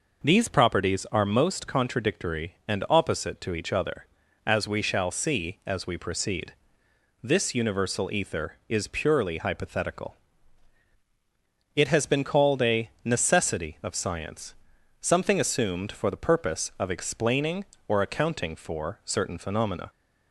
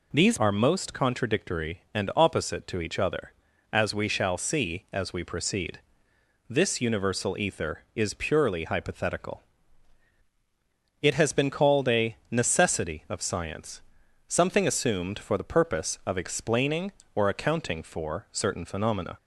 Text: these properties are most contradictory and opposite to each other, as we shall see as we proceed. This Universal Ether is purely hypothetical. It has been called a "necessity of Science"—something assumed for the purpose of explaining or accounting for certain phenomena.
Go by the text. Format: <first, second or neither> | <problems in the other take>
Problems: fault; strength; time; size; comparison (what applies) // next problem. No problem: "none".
first | skips "properties"; at 0.3 s